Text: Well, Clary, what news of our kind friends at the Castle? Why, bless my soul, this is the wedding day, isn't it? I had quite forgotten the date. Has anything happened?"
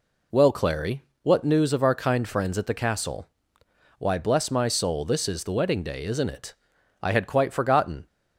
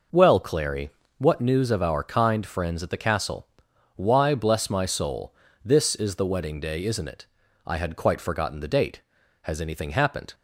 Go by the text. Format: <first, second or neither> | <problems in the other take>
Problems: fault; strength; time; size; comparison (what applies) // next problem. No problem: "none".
second | stops before "the date Has anything happened"; at 8.0 s